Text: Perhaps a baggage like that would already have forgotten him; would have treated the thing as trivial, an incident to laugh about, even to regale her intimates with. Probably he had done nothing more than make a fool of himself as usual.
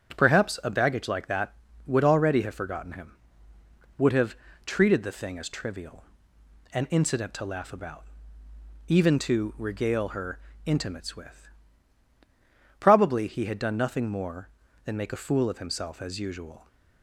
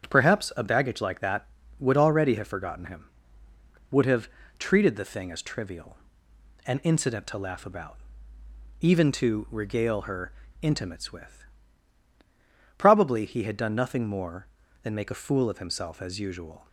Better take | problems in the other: neither | starts louder than the rest; strong; the same in both // pauses between "have" and "treated"; slight; the same in both // pauses between "her" and "intimates"; slight; the same in both

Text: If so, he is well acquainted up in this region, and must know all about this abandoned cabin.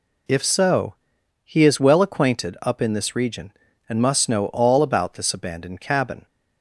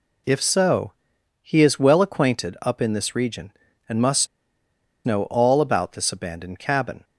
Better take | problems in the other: first | pauses between "must" and "know"; noticeable; at 4.2 s; 0.78 s long

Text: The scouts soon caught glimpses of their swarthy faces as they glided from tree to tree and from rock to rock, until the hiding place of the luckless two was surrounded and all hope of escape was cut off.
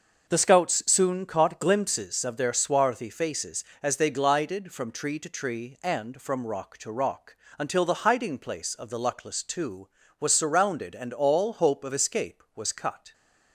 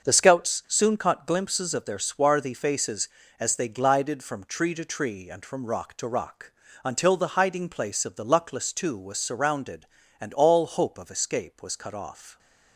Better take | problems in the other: second | starts louder than the rest; until 1.3 s; 6 dB; also in the second // stops before "off"; at 13.1 s

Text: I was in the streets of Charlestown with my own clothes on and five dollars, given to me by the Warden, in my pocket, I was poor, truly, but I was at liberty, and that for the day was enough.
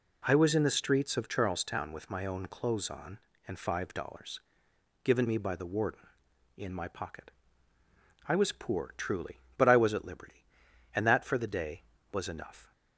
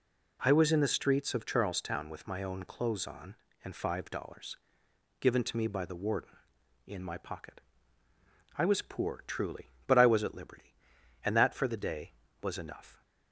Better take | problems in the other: second | skips "to"; at 5.2 s

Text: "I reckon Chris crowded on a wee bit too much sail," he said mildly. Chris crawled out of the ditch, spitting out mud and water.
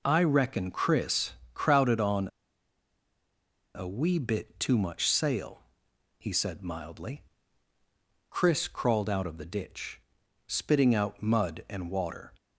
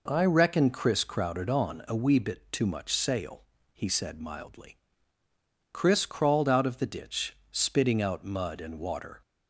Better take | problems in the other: second | pauses between "Chris" and "crowded"; slight; at 1.3 s; 0.20 s long // pauses between "on" and "a"; strong; at 2.2 s; 1.4 s long

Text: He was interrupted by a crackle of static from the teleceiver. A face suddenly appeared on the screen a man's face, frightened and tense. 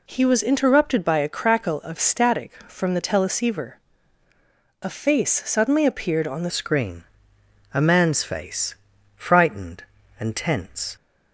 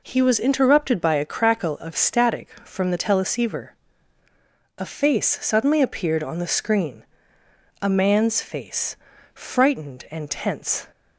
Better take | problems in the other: second | changes voice at "screen"; from 6.4 s on; 4.5 s long // pauses between "screen" and "a"; noticeable; at 7.0 s; 0.70 s long; noticeable in the second

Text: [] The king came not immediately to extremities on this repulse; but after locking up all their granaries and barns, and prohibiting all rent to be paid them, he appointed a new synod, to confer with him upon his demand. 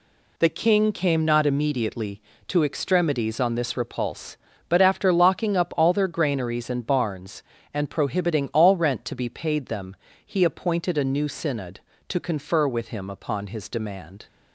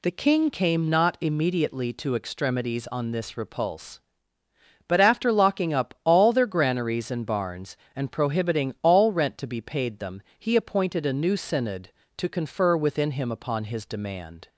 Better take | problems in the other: first | says "within" for "with"; at 12.7 s

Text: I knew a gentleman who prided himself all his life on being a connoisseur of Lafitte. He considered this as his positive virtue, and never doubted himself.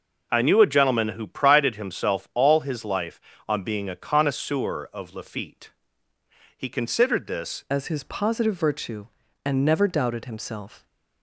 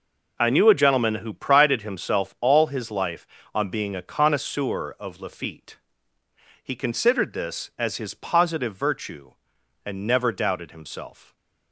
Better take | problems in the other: second | changes voice at "as"; from 7.6 s on; 3.2 s long

